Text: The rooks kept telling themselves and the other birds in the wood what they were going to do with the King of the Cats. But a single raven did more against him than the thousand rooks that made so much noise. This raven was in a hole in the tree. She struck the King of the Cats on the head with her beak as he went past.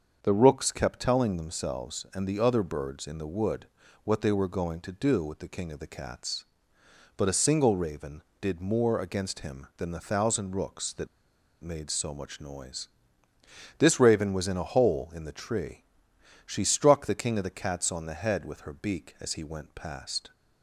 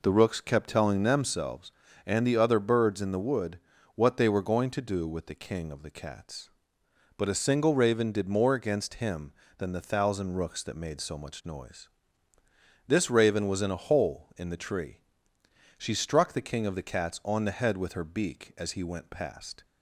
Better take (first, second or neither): second